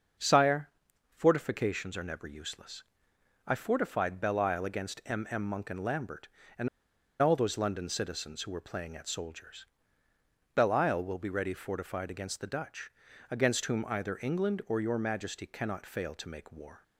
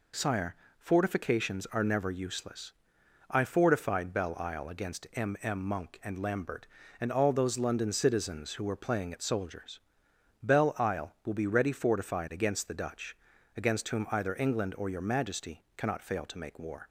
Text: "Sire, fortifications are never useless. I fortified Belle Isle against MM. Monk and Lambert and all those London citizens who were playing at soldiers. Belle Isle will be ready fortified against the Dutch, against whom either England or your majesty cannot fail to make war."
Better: second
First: starts louder than the rest; until 1.6 s; 6.5 dB // pauses between "and" and "all"; noticeable; at 6.6 s; 0.54 s long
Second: none

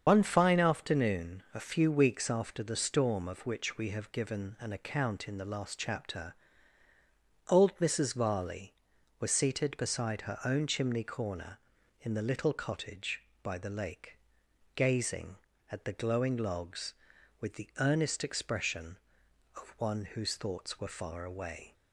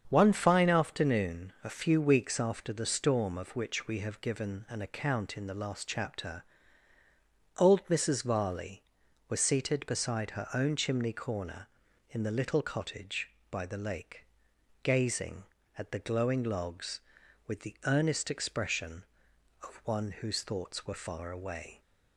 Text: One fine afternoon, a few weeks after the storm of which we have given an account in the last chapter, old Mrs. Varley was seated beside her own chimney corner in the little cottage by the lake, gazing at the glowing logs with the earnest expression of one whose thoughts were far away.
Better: second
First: loses the start of "One"; at 0.0 s; 115 ms // starts louder than the rest; strong; until 1.0 s; 7 dB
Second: starts louder than the rest; strong; until 1.0 s; 7.5 dB

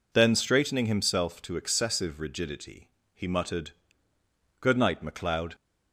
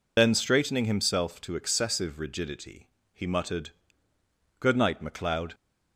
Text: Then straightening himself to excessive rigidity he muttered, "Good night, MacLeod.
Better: first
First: pauses between "rigidity" and "he"; slight; at 2.9 s; 0.24 s long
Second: loses the start of "Then"; at 0.1 s; 55 ms // pauses between "rigidity" and "he"; slight; at 2.8 s; 0.24 s long

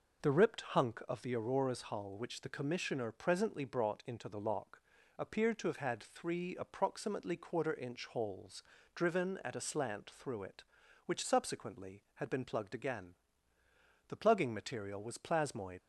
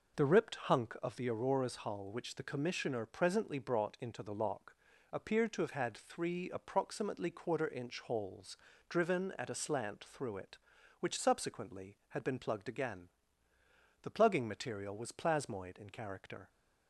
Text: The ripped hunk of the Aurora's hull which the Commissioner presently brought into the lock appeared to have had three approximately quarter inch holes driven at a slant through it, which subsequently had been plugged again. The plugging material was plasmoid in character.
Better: second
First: pauses between "lock" and "appeared"; at 4.8 s; 0.38 s long // pauses between "holes" and "driven"; slight; at 8.6 s; 0.32 s long // stops before "in character"; at 15.8 s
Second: pauses between "lock" and "appeared"; at 4.7 s; 0.38 s long // pauses between "holes" and "driven"; slight; at 8.5 s; 0.32 s long

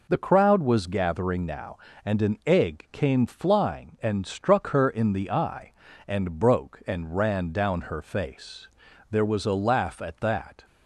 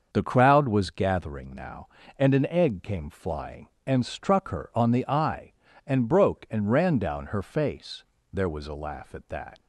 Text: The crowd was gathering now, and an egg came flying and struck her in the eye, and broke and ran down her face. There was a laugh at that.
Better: first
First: none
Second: starts louder than the rest; until 1.1 s; 6.5 dB // says "on" for "in"; at 4.7 s

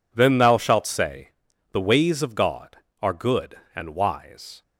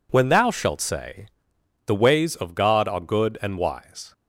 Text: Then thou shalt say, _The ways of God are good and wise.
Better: first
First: none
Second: says "When" for "Then"; at 0.1 s

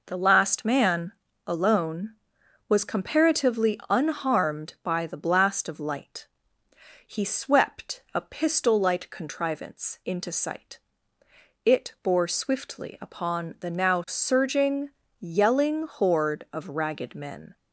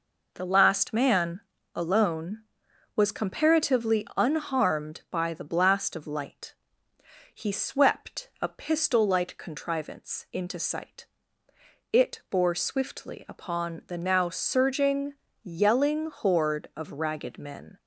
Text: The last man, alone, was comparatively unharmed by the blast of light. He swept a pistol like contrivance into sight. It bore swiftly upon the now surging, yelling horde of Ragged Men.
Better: neither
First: none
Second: none

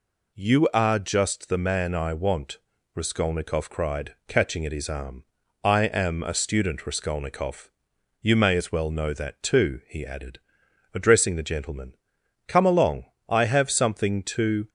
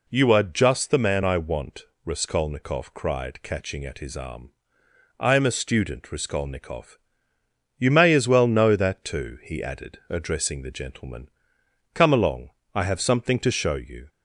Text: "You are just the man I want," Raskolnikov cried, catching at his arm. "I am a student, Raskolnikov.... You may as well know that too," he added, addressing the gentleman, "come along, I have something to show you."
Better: second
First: stops before "show you"; at 14.6 s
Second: none

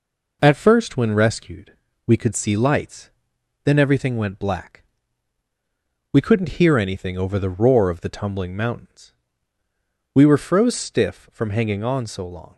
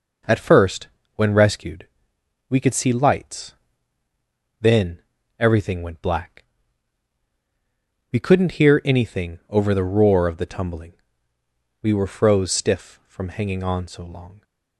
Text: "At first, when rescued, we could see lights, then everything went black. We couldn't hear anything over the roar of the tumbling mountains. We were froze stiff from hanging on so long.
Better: first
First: none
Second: pauses between "then" and "everything"; slight; at 5.0 s; 0.36 s long // skips "mountains"; at 11.3 s

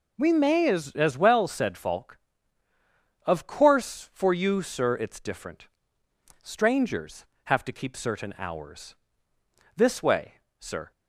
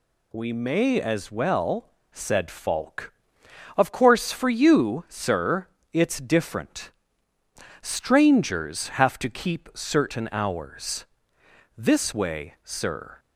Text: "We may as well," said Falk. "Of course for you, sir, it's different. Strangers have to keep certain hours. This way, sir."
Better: second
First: says "as" twice; at 0.9 s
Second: none

